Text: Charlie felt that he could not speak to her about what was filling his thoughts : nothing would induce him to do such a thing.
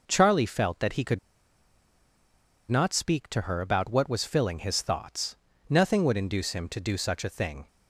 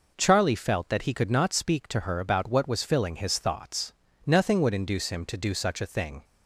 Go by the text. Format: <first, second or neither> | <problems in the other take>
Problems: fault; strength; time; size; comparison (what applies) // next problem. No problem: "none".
second | pauses between "could" and "not"; strong; at 1.1 s; 1.5 s long